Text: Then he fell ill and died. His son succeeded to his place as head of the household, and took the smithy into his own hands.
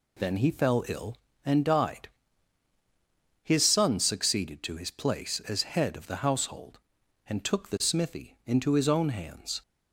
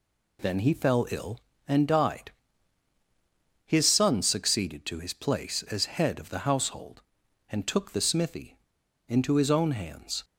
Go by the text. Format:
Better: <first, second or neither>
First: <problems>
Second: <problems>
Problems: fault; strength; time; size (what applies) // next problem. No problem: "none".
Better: first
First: none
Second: pauses between "smithy" and "into"; noticeable; at 8.5 s; 0.51 s long